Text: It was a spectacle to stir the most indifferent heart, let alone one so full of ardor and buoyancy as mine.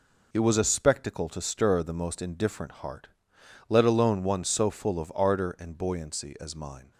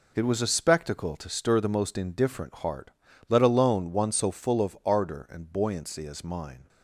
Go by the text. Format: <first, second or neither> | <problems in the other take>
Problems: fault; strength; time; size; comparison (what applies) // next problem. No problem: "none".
neither | none